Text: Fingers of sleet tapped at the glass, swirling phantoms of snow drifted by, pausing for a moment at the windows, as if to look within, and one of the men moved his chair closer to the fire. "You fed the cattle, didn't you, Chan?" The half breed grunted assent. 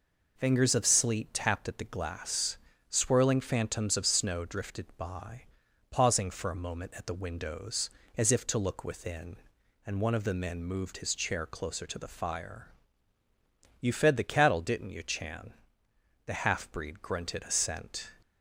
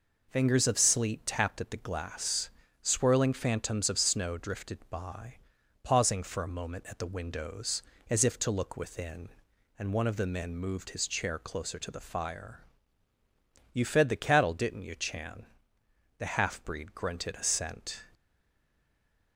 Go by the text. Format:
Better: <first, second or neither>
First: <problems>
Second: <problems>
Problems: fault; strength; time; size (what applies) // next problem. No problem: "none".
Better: first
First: none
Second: stays silent after the last word; noticeable; from 18.1 s on; 1.2 s long